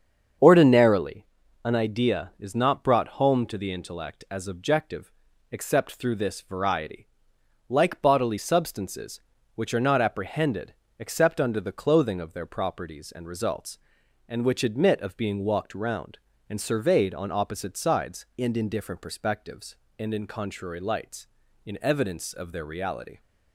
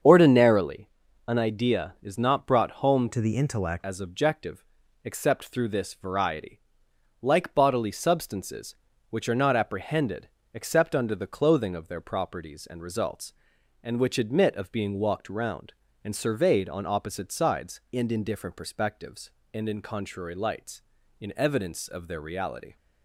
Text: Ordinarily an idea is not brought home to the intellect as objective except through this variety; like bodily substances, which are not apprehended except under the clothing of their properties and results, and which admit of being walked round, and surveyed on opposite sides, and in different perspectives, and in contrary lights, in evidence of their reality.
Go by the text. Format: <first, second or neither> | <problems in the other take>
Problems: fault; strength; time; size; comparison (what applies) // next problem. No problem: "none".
first | starts louder than the rest; strong; until 1.4 s; 7.5 dB; strong in the first // pauses between "Ordinarily" and "an"; at 0.8 s; 0.40 s long; also in the first // changes voice from "to" to "intellect"; from 3.1 to 3.8 s; 0.7 s long // pauses between "objective" and "except"; at 4.6 s; 0.40 s long; also in the first // pauses between "apprehended" and "except"; slight; at 10.2 s; 0.24 s long; slight in the first